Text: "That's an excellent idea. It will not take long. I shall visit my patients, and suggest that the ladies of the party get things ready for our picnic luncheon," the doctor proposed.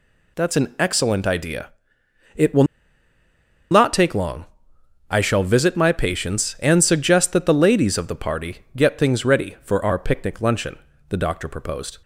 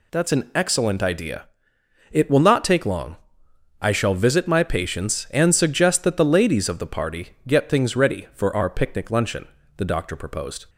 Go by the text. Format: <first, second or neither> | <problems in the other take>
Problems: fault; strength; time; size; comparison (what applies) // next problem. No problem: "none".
second | pauses between "will" and "not"; at 2.6 s; 1.0 s long